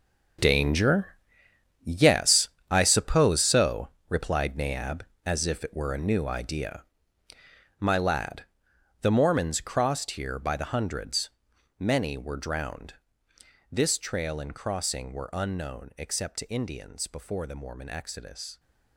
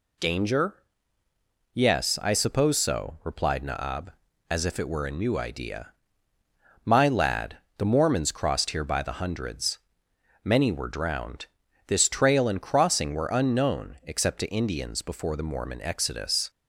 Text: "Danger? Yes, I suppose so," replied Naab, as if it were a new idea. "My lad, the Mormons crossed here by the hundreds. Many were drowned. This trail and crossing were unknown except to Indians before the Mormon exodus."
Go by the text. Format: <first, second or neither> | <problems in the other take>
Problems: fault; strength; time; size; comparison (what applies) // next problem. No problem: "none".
second | gets quieter; strong; throughout; 13 dB